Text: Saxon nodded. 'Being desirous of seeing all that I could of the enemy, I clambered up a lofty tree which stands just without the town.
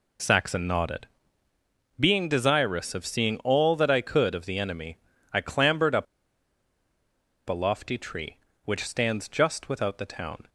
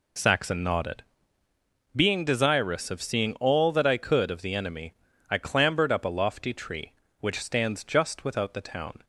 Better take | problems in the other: second | pauses between "up" and "a"; strong; at 6.0 s; 1.4 s long

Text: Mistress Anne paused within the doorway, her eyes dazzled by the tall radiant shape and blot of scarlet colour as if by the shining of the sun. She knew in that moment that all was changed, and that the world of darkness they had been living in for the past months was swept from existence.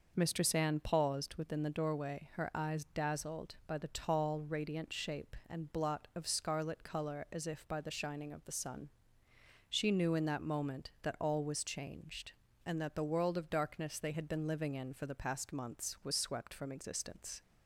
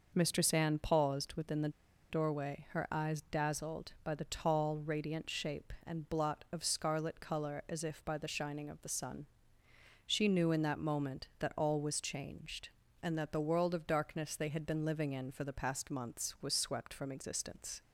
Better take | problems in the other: first | pauses between "the" and "doorway"; at 1.6 s; 0.40 s long

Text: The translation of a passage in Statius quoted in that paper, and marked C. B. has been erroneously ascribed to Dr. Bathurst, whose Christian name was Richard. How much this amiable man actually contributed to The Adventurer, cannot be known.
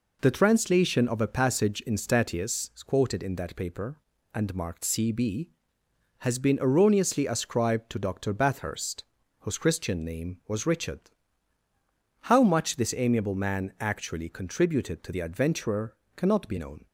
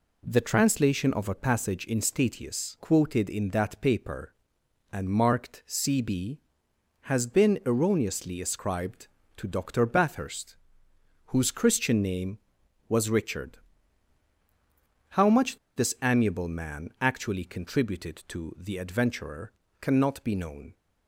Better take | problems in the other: first | pauses between "much" and "this"; slight; at 15.5 s; 0.18 s long

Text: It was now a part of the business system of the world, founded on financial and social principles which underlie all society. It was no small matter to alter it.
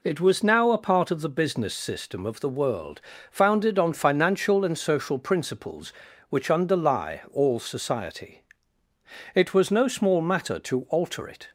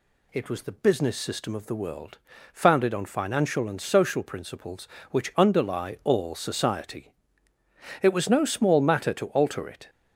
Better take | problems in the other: first | skips "now a part of"; at 0.6 s

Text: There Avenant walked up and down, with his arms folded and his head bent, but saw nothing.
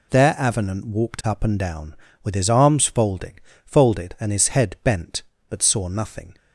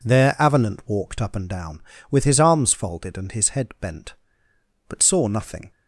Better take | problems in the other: second | says "folded" twice; at 3.6 s

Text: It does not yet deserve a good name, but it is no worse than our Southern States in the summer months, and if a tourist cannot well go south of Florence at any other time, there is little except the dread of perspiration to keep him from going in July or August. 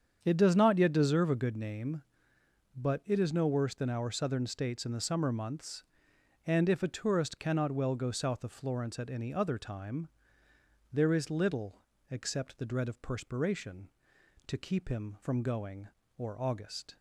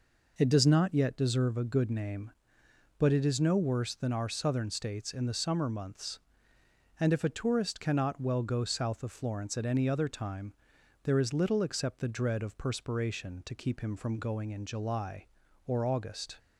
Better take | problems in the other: second | starts louder than the rest; strong; until 1.2 s; 8 dB // pauses between "little" and "except"; slight; at 11.7 s; 0.34 s long // skips "in July"; at 16.0 s

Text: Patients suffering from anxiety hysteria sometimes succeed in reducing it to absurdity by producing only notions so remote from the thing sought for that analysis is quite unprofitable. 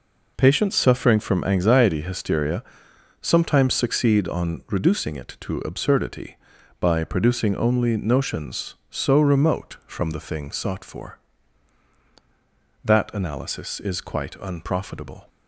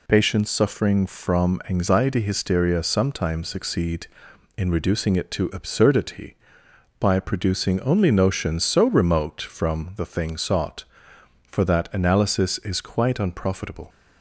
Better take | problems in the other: second | pauses between "hysteria" and "sometimes"; noticeable; at 2.6 s; 0.58 s long // says "on" for "in"; at 4.2 s

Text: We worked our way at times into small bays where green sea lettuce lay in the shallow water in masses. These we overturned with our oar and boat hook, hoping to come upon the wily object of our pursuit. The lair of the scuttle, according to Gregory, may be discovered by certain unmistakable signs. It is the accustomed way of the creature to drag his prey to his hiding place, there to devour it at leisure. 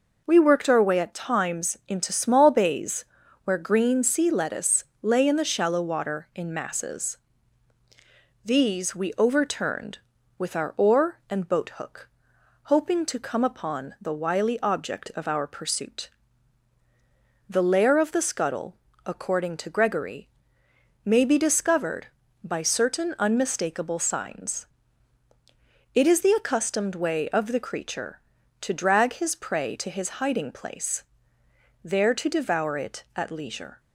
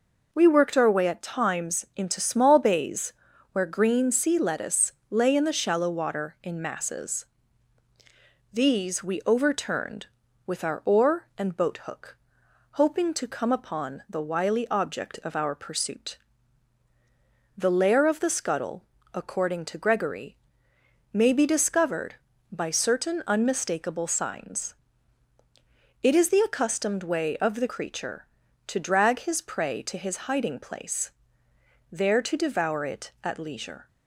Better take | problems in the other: neither | pauses between "bays" and "where"; the same in both // pauses between "lettuce" and "lay"; slight; the same in both

